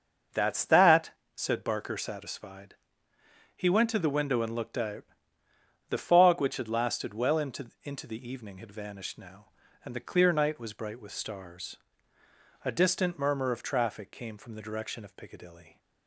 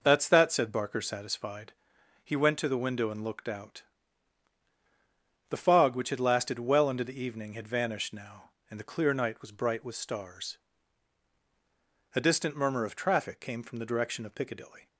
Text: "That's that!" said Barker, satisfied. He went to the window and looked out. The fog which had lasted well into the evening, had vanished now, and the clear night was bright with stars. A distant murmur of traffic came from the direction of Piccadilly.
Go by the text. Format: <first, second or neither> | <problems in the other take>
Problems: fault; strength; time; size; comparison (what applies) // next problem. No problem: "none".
second | starts louder than the rest; until 1.5 s; 6.5 dB // says "into" twice; at 7.8 s